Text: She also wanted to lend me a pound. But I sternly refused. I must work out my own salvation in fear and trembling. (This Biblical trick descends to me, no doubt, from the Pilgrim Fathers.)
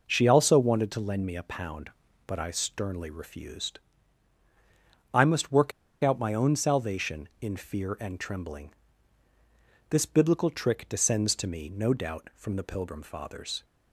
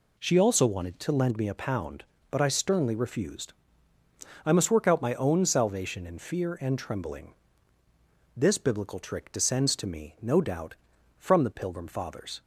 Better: second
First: pauses between "work" and "out"; slight; at 5.7 s; 0.32 s long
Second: none

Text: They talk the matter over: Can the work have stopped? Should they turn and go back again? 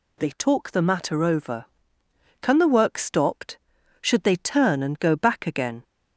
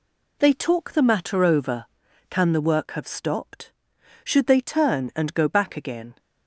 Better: second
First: skips "have"; at 2.9 s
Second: none

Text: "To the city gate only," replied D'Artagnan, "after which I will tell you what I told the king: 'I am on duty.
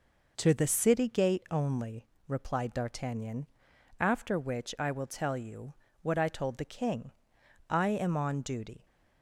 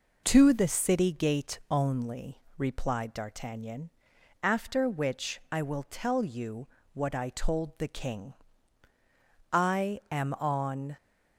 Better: first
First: pauses between "you" and "what"; slight; at 5.7 s; 0.26 s long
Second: pauses between "you" and "what"; slight; at 6.6 s; 0.28 s long // stops before "duty"; at 10.9 s

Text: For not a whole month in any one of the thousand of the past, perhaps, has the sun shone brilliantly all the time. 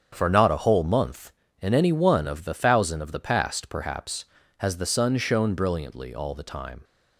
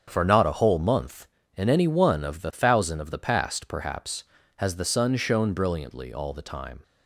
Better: neither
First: starts louder than the rest; strong; until 1.1 s; 8 dB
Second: starts louder than the rest; strong; until 1.0 s; 8 dB

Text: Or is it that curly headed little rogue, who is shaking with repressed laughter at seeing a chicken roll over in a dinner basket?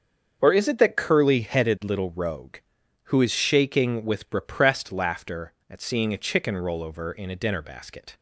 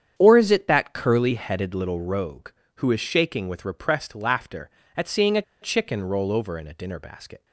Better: first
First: starts louder than the rest; until 1.4 s; 7 dB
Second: starts louder than the rest; strong; until 1.1 s; 8.5 dB // pauses between "a" and "chicken"; slight; at 5.4 s; 0.20 s long

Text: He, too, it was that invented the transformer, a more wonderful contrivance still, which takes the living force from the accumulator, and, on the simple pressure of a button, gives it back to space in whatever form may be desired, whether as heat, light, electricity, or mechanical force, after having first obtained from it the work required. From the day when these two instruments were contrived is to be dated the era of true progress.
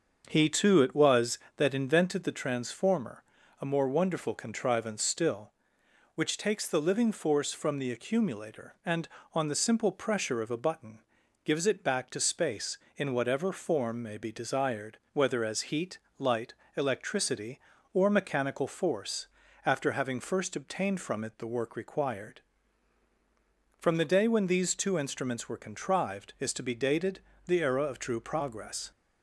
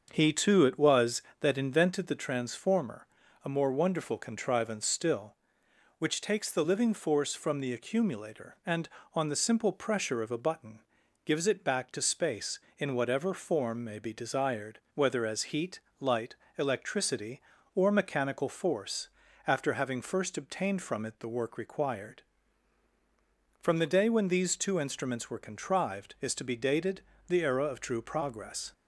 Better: neither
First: starts louder than the rest; until 1.2 s; 6.5 dB // pauses between "dated" and "the"; slight; at 27.1 s; 0.26 s long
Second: starts louder than the rest; until 1.1 s; 6.5 dB // pauses between "dated" and "the"; slight; at 27.0 s; 0.26 s long

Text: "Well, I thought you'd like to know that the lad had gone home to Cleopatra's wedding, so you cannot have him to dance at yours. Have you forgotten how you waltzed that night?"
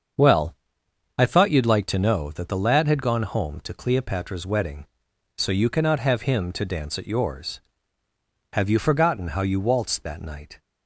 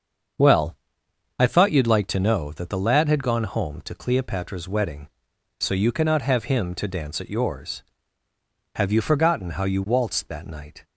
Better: neither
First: starts louder than the rest; until 1.8 s; 7 dB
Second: starts louder than the rest; until 2.0 s; 7 dB

